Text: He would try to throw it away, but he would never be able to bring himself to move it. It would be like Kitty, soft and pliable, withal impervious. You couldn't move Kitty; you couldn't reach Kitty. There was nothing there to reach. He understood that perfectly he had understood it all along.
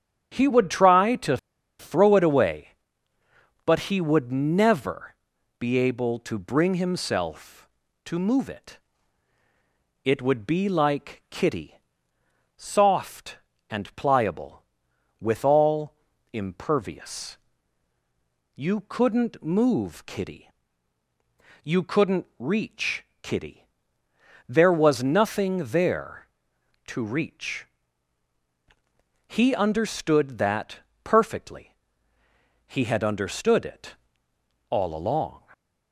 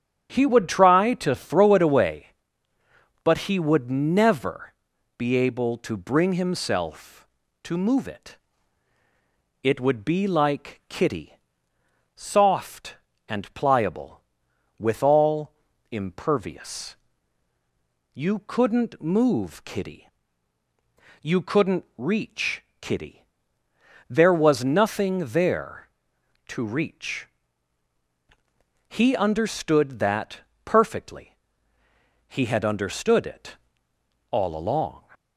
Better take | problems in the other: second | starts louder than the rest; strong; until 1.3 s; 9.5 dB; strong in the second // pauses between "to" and "throw"; at 1.3 s; 0.42 s long // pauses between "never" and "be"; noticeable; at 5.1 s; 0.46 s long; noticeable in the second // pauses between "withal" and "impervious"; at 15.9 s; 0.40 s long; also in the second // pauses between "reach" and "Kitty"; slight; at 23.0 s; 0.16 s long; slight in the second // pauses between "that" and "perfectly"; slight; at 30.8 s; 0.24 s long; slight in the second // pauses between "perfectly" and "he"; noticeable; at 31.7 s; 0.92 s long; noticeable in the second // pauses between "it" and "all"; noticeable; at 33.9 s; 0.74 s long; noticeable in the second

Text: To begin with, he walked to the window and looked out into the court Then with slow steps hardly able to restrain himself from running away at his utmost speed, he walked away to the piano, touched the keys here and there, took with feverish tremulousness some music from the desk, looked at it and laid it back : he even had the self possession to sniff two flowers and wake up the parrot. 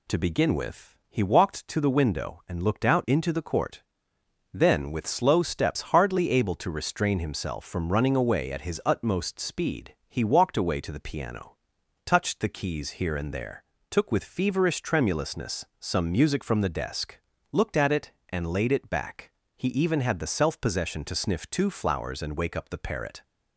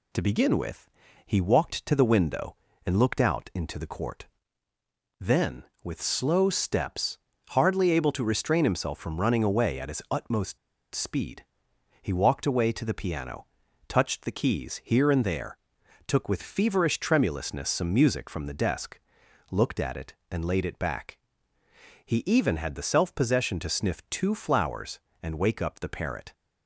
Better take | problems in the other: first | pauses between "court" and "Then"; noticeable; at 4.2 s; 0.92 s long; noticeable in the first // pauses between "steps" and "hardly"; slight; at 7.1 s; 0.34 s long // pauses between "utmost" and "speed"; at 10.5 s; 0.36 s long

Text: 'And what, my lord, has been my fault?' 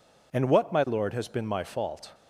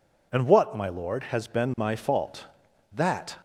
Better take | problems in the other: first | goes on to say "That"; slight; from 2.9 s on; 0.42 s long

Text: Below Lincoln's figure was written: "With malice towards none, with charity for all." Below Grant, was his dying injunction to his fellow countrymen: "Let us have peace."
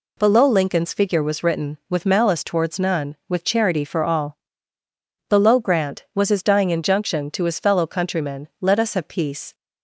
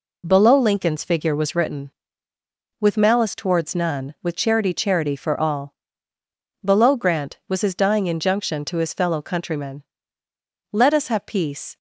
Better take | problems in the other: first | says "charity" twice; at 4.7 s

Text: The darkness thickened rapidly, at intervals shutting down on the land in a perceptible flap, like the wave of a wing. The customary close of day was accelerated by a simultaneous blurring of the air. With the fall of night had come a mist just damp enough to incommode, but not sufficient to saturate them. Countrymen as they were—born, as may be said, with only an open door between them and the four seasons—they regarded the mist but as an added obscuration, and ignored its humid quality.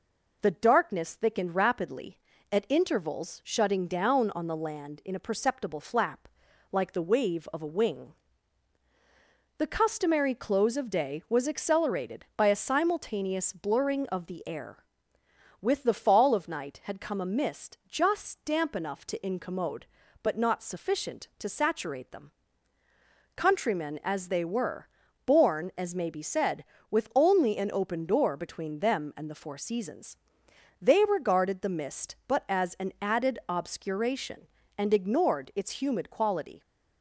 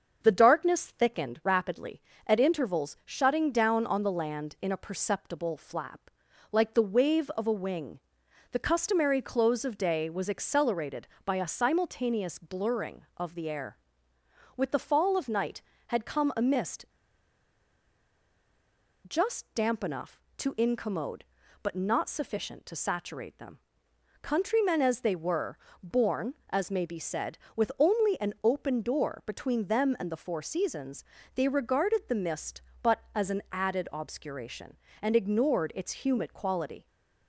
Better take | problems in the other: first | starts louder than the rest; until 1.2 s; 6.5 dB // pauses between "mist" and "just"; strong; at 16.8 s; 2.2 s long

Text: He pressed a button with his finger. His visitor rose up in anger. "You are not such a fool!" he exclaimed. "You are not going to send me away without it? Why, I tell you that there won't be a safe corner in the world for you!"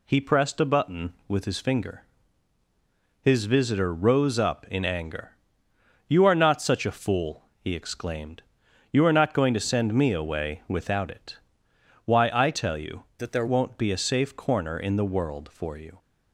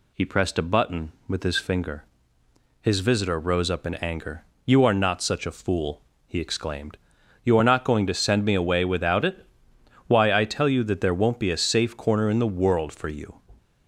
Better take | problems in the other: second | changes voice from "that" to "there"; from 13.1 to 13.4 s; 0.3 s long

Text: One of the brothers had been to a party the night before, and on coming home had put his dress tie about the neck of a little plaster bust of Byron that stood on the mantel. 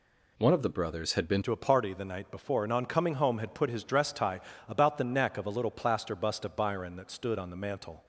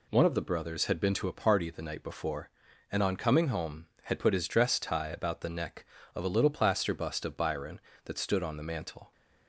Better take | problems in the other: second | changes voice at "to"; from 1.4 s on; 6.6 s long // pauses between "tie" and "about"; slight; at 4.4 s; 0.26 s long

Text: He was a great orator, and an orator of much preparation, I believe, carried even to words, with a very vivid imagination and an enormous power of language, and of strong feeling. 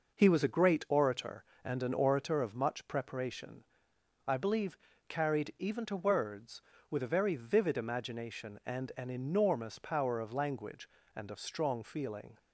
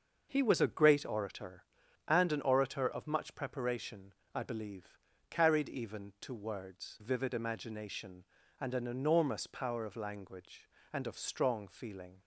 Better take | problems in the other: first | starts louder than the rest; noticeable; until 1.3 s; 6 dB // skips "with a very"; at 6.9 s

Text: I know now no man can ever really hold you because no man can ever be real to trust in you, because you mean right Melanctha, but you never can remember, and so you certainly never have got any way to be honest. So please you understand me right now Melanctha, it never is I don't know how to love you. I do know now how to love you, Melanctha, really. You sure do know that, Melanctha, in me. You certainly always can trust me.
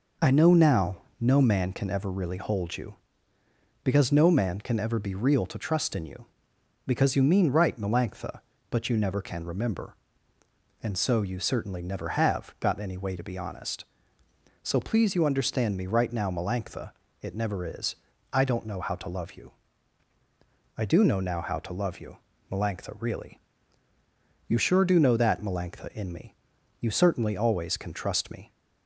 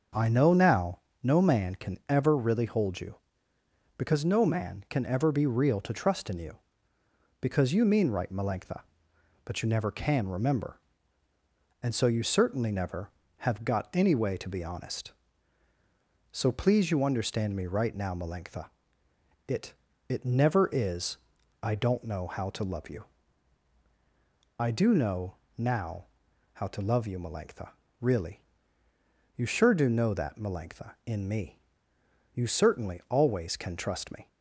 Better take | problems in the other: first | starts louder than the rest; until 1.4 s; 6.5 dB // pauses between "now" and "no"; slight; at 0.9 s; 0.24 s long; slight in the first // says "it" twice; at 20.0 s // pauses between "is" and "I"; at 21.1 s; 0.42 s long; also in the first // pauses between "know" and "now"; slight; at 25.3 s; 0.24 s long // pauses between "now" and "how"; noticeable; at 26.0 s; 0.48 s long

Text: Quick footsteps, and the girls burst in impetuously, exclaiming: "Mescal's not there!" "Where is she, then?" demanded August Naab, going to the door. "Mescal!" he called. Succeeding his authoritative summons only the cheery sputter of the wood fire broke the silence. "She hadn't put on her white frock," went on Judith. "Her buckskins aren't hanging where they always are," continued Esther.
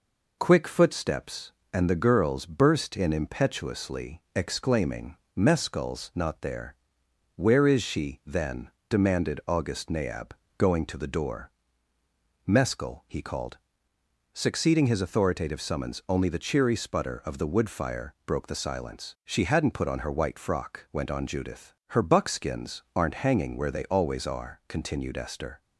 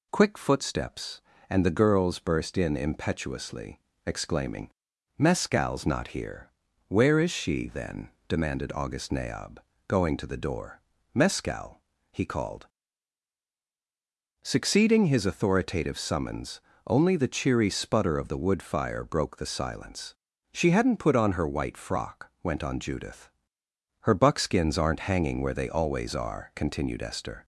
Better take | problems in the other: first | says "here" for "there"; at 6.0 s // pauses between "summons" and "only"; slight; at 16.5 s; 0.28 s long

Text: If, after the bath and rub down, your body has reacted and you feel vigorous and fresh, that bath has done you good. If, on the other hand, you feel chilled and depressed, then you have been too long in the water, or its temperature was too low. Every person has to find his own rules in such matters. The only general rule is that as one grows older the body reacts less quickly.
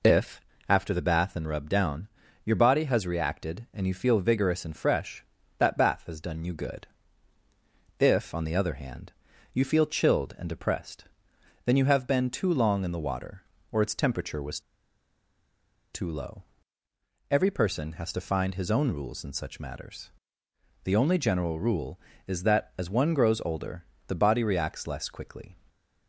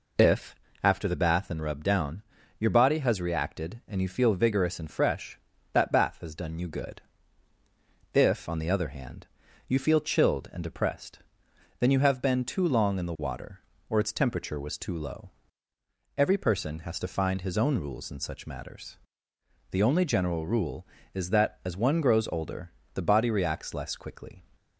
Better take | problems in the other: second | pauses between "was" and "too"; strong; at 14.5 s; 1.3 s long // pauses between "older" and "the"; slight; at 23.8 s; 0.24 s long; slight in the second

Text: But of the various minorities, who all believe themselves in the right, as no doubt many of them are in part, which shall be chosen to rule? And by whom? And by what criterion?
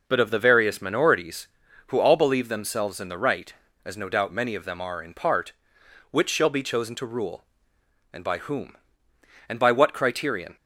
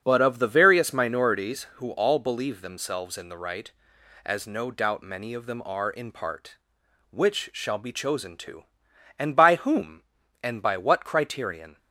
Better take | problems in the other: first | starts louder than the rest; until 1.0 s; 7 dB // skips "rule"; at 8.9 s

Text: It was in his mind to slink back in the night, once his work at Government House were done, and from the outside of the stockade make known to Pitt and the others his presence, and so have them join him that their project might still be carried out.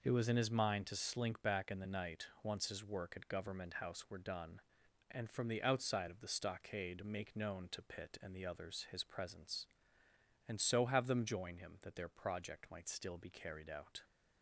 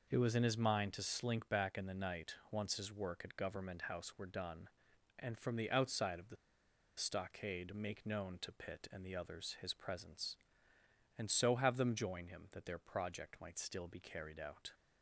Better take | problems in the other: first | pauses between "the" and "stockade"; noticeable; at 6.3 s; 0.62 s long

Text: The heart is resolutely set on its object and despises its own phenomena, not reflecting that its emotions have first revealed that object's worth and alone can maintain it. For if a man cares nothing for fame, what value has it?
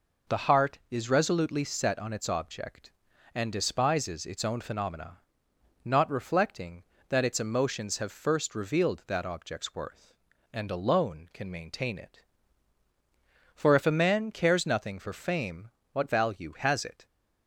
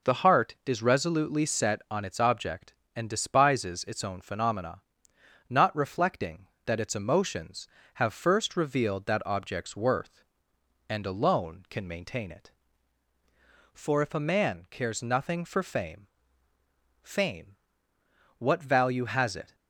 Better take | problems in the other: first | says "fame" twice; at 17.0 s

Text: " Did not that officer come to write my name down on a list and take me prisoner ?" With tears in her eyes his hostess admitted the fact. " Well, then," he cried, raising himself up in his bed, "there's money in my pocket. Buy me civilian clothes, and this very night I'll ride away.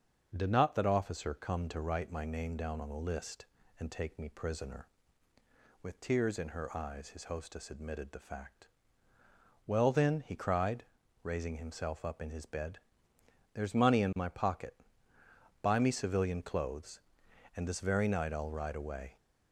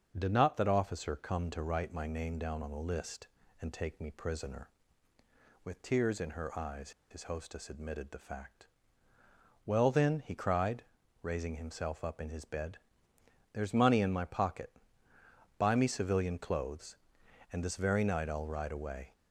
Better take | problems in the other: first | starts louder than the rest; strong; until 1.1 s; 11.5 dB; strong in the first // pauses between "eyes" and "his"; slight; at 6.9 s; 0.20 s long

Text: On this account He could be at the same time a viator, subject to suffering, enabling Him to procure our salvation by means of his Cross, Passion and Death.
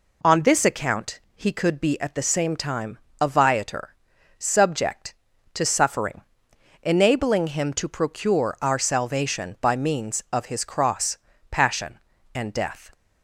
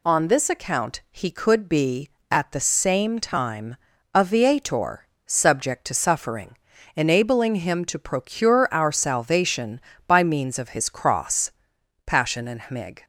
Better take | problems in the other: first | pauses between "time" and "a"; slight; at 3.7 s; 0.36 s long; slight in the first // says "Hmig" for "Death"; at 12.5 s

